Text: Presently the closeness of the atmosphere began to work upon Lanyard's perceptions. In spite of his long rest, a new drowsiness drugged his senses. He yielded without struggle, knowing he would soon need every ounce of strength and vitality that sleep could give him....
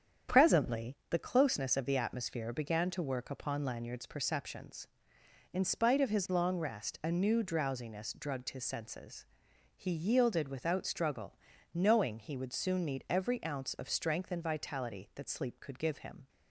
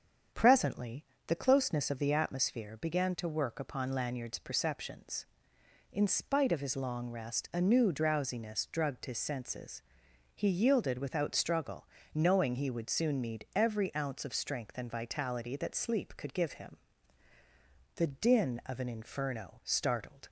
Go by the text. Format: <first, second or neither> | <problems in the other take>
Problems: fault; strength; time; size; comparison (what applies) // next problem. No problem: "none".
first | starts louder than the rest; strong; until 1.5 s; 7.5 dB; strong in the first // pauses between "Presently" and "the"; slight; at 1.0 s; 0.22 s long // goes on to say "The din of an inferno startled"; strong; from 17.9 s on; 2.3 s long